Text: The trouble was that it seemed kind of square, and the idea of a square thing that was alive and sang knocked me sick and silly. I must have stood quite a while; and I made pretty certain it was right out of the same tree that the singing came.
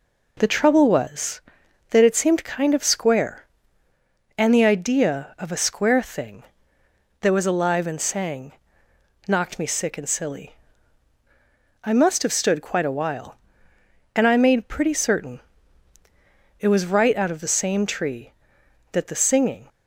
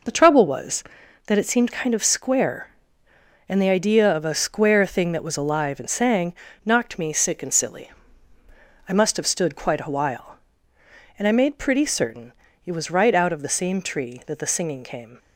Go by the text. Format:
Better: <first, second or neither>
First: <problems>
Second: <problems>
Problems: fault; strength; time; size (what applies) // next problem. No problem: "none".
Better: second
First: pauses between "sang" and "knocked"; noticeable; at 8.5 s; 0.74 s long // pauses between "certain" and "it"; at 15.4 s; 1.2 s long // stops before "came"; at 19.6 s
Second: pauses between "sang" and "knocked"; slight; at 6.3 s; 0.32 s long // pauses between "certain" and "it"; slight; at 12.3 s; 0.32 s long